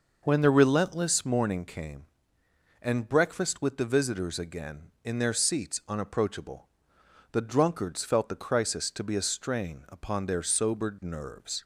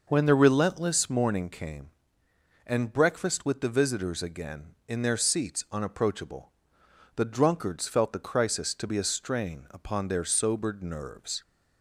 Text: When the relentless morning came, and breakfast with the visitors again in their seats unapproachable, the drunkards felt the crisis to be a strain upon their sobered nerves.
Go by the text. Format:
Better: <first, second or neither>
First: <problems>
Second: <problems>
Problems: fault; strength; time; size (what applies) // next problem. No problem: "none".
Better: neither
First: none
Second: none